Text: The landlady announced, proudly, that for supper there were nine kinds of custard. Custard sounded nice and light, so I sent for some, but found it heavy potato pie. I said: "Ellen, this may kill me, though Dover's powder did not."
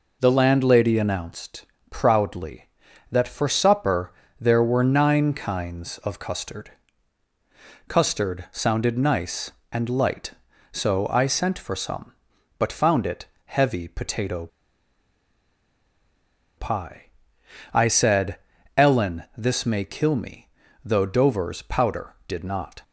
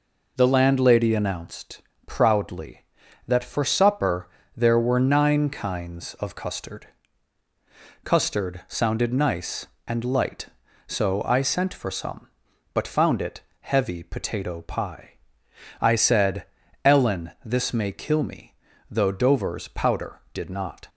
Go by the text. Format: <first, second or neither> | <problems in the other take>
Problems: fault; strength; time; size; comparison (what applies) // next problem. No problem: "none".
second | pauses between "supper" and "there"; slight; at 4.1 s; 0.26 s long; slight in the second // pauses between "it" and "heavy"; slight; at 13.2 s; 0.20 s long; slight in the second // pauses between "potato" and "pie"; strong; at 14.4 s; 2.1 s long